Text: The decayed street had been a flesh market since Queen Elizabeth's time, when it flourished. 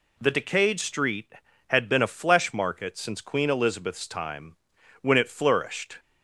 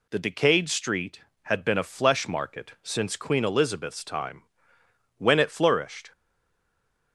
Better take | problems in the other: first | stays silent after the last word; from 6.1 s on; 1.0 s long

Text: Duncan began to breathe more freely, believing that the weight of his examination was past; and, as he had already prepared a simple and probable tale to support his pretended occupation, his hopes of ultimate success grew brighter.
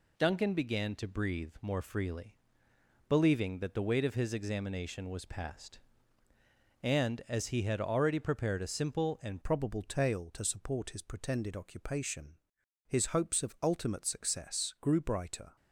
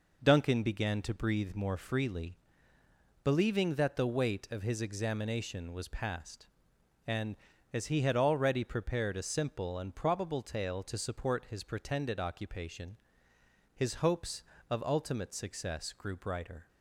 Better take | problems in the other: second | changes voice at "probable"; from 9.4 s on; 6.1 s long

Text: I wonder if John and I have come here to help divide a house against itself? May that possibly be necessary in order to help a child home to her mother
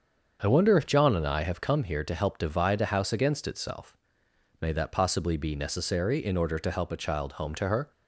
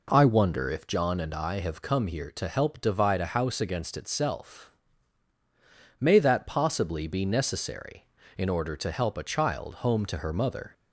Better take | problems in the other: second | starts louder than the rest; until 1.4 s; 7 dB // stops before "mother"; at 7.9 s

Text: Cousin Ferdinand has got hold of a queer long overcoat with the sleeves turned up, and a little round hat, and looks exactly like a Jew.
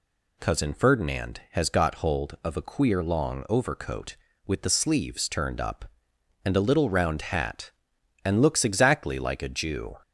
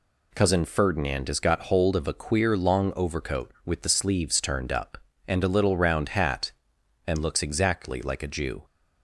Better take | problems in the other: neither | none

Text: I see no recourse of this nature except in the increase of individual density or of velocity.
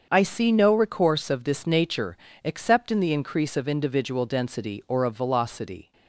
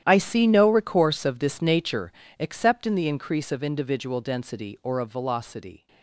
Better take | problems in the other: first | gets quieter; strong; throughout; 16.5 dB // starts louder than the rest; strong; until 1.0 s; 11 dB; also in the first // pauses between "nature" and "except"; slight; at 2.1 s; 0.26 s long; slight in the first

